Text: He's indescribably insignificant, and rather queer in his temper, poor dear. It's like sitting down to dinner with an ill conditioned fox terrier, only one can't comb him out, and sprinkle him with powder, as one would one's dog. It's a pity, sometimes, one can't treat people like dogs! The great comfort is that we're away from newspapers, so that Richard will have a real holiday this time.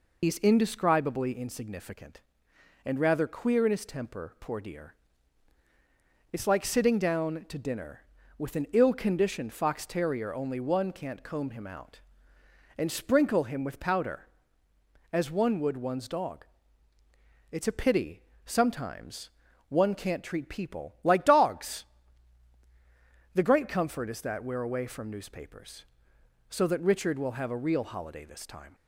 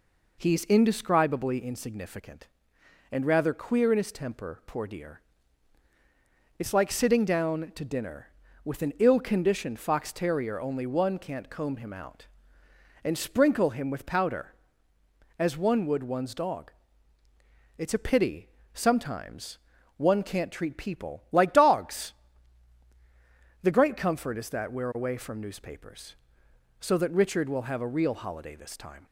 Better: second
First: loses the start of "He's"; at 0.2 s; 100 ms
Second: none

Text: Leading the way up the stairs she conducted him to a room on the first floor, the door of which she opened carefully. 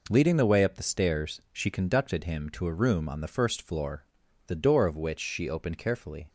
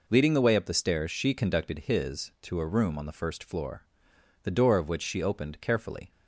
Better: first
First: none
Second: says "his" for "him"; at 1.7 s

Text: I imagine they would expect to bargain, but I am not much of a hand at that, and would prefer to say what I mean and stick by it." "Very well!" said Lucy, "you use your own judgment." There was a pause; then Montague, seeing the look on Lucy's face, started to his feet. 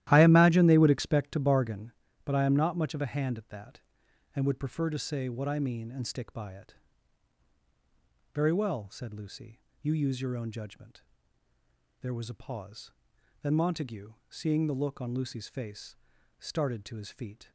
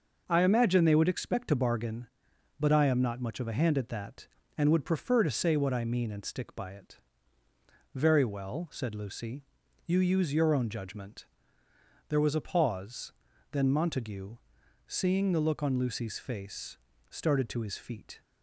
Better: second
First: starts louder than the rest; strong; until 1.9 s; 14 dB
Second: none

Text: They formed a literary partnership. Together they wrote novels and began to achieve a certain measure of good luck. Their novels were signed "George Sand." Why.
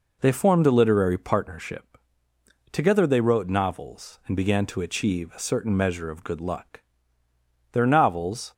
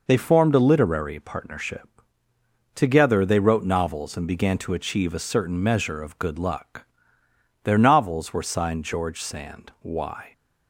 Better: second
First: stops before "were signed George Sand Why"; at 8.5 s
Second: none

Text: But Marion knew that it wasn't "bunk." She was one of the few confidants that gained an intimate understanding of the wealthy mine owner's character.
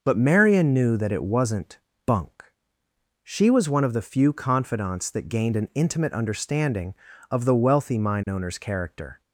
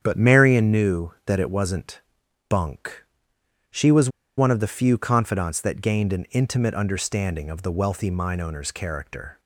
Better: first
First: pauses between "wasn't" and "bunk"; slight; at 1.7 s; 0.28 s long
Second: starts louder than the rest; strong; until 1.0 s; 8.5 dB // pauses between "wasn't" and "bunk"; noticeable; at 2.0 s; 0.48 s long // pauses between "was" and "one"; slight; at 4.0 s; 0.28 s long

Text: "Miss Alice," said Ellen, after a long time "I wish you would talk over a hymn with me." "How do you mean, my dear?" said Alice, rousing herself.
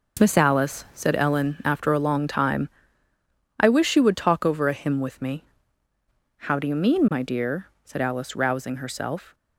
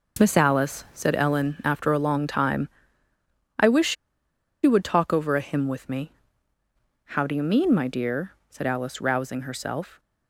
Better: first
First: pauses between "time" and "I"; noticeable; at 2.6 s; 0.90 s long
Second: pauses between "time" and "I"; noticeable; at 2.6 s; 0.90 s long // pauses between "wish" and "you"; noticeable; at 3.9 s; 0.68 s long

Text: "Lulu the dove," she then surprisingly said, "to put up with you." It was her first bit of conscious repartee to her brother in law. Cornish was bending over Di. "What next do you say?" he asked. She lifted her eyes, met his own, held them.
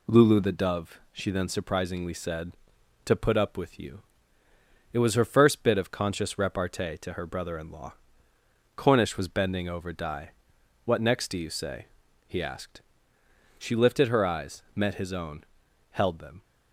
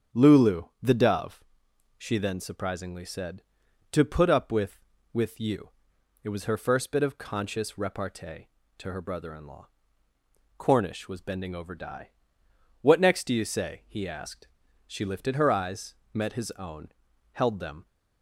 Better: first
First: none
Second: starts louder than the rest; strong; until 1.3 s; 8 dB // pauses between "Lulu" and "the"; slight; at 0.6 s; 0.18 s long // says "with" twice; at 5.1 s

